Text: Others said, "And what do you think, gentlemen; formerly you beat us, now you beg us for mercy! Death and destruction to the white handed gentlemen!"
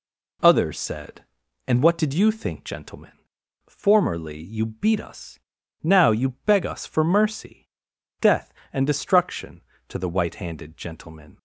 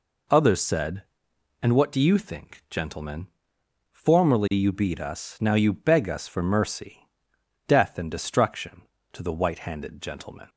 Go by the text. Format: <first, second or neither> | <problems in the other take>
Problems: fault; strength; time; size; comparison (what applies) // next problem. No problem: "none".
second | says "did" for "do"; at 1.9 s // pauses between "you" and "beg"; slight; at 6.2 s; 0.16 s long